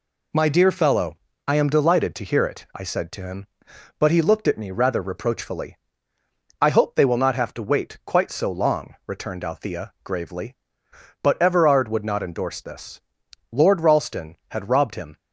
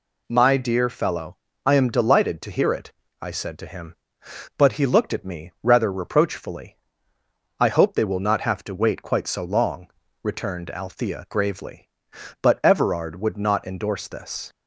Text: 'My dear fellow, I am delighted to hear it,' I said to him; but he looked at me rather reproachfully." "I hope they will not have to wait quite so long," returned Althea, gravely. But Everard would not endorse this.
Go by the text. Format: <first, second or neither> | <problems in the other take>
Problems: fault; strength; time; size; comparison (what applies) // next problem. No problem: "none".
second | goes on to say "Lord Ralston had robbed him"; from 13.5 s on; 1.6 s long